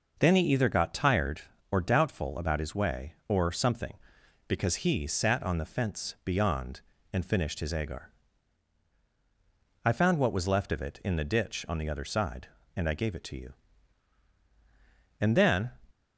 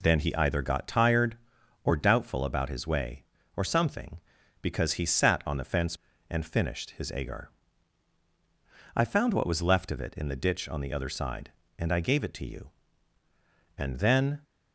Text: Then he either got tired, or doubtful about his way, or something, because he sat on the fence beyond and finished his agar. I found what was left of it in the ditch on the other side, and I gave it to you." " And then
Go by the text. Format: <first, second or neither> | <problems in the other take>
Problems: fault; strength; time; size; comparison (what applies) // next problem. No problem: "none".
first | skips "beyond"; at 6.1 s